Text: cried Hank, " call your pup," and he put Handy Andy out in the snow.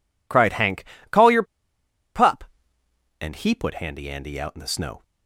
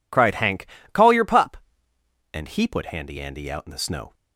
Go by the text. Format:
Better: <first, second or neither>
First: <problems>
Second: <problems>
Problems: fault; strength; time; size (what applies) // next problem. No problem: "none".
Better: second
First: pauses between "your" and "pup"; noticeable; at 1.4 s; 0.72 s long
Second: none